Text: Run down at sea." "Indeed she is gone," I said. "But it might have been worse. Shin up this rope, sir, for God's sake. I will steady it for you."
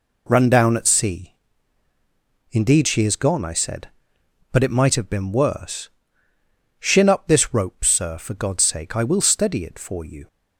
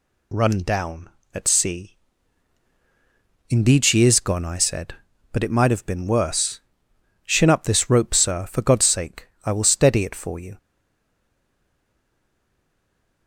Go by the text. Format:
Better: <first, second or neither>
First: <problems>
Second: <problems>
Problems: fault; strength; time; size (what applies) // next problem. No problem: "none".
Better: first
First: none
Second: stays silent after the last word; strong; from 10.5 s on; 2.7 s long